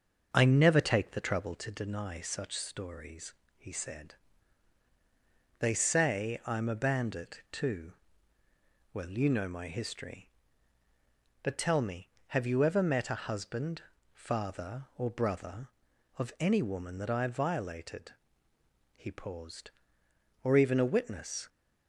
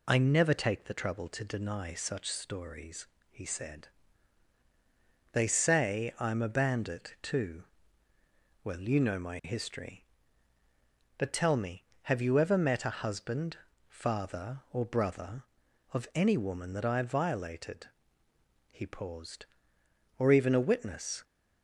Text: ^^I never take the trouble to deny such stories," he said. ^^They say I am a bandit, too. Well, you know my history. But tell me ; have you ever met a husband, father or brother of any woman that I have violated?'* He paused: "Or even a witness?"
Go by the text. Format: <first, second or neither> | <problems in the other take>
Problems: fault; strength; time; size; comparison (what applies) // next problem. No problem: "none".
second | starts louder than the rest; until 1.7 s; 6.5 dB